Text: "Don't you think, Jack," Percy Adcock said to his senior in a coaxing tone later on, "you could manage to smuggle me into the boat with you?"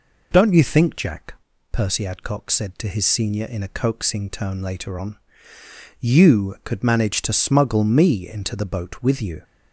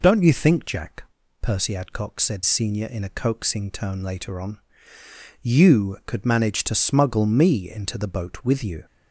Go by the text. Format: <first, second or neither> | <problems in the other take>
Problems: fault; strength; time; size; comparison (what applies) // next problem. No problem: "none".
first | skips "to his"; at 2.4 s